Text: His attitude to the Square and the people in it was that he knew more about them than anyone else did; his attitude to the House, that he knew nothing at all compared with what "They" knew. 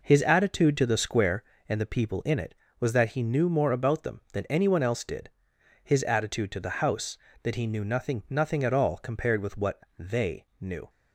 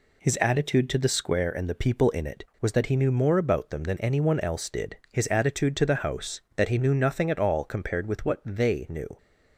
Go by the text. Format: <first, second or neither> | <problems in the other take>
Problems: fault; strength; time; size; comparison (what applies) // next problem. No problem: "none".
second | says "nothing" twice; at 8.2 s // pauses between "what" and "They"; slight; at 9.8 s; 0.16 s long // pauses between "They" and "knew"; slight; at 10.4 s; 0.16 s long